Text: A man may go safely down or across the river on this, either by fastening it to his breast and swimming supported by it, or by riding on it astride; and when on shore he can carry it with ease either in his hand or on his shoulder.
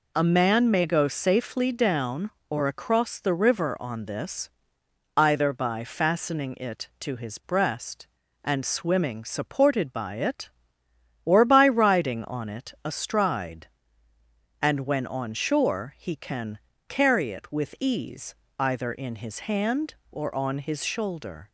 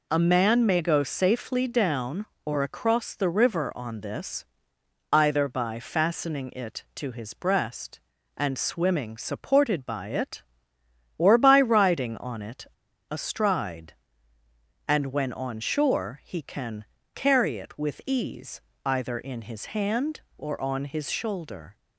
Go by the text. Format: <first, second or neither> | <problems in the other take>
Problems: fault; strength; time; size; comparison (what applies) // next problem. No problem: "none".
first | pauses between "it" and "astride"; at 12.6 s; 0.45 s long // pauses between "can" and "carry"; slight; at 16.8 s; 0.30 s long; slight in the first // pauses between "ease" and "either"; slight; at 18.6 s; 0.24 s long; slight in the first